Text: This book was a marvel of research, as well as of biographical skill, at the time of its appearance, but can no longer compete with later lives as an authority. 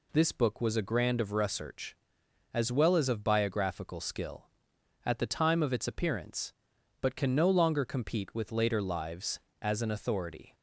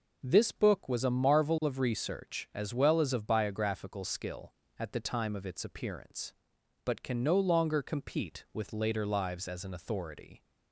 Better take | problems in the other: second | says "grand" for "marvel"; at 0.8 s

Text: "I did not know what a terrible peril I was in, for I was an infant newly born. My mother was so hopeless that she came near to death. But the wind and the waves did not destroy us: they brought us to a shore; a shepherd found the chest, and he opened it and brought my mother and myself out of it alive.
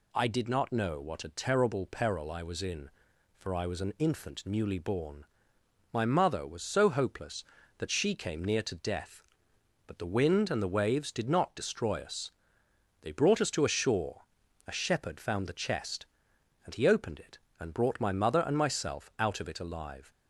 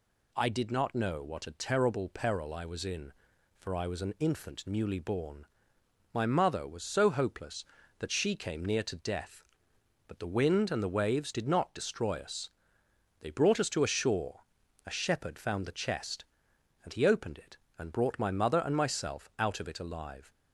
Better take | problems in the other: neither | none

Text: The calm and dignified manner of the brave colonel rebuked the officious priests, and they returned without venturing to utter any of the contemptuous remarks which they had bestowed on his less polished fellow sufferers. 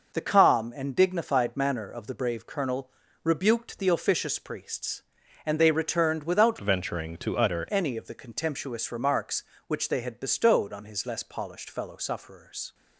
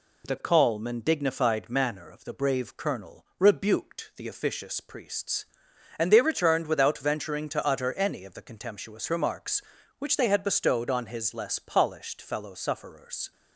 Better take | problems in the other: second | pauses between "colonel" and "rebuked"; slight; at 2.8 s; 0.34 s long // changes voice from "venturing" to "utter"; from 6.6 to 7.6 s; 1.0 s long

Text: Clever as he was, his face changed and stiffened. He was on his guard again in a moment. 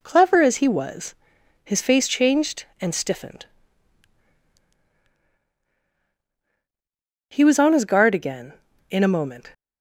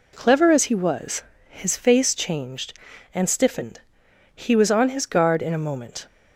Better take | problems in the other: first | skips "again"; at 5.4 s

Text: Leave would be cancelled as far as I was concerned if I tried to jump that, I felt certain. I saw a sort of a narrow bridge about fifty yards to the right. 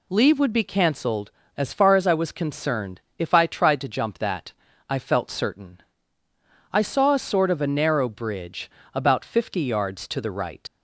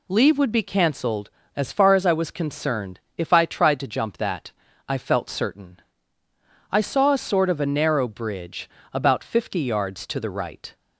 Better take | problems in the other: second | pauses between "concerned" and "if"; slight; at 2.9 s; 0.18 s long; slight in the second // pauses between "bridge" and "about"; slight; at 8.6 s; 0.24 s long; slight in the second // leaves "right" unfinished; at 10.6 s; 80 ms

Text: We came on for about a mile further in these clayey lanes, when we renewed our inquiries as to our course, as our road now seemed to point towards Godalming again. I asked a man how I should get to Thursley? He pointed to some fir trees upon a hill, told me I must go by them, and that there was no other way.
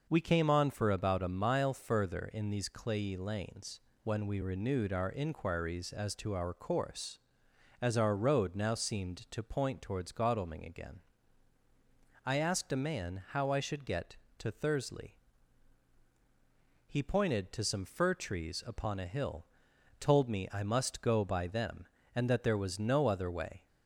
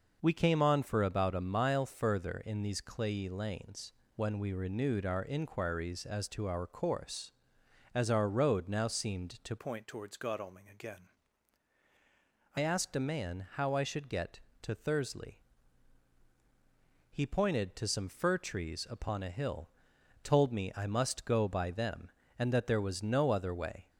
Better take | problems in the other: first | changes voice from "point" to "I"; from 9.5 to 12.5 s; 3.0 s long

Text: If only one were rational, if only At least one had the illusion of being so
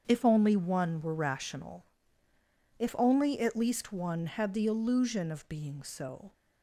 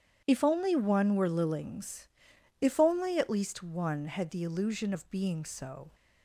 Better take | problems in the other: first | starts louder than the rest; strong; until 1.2 s; 9.5 dB; strong in the first // says "lillings" for "rational"; at 1.2 s

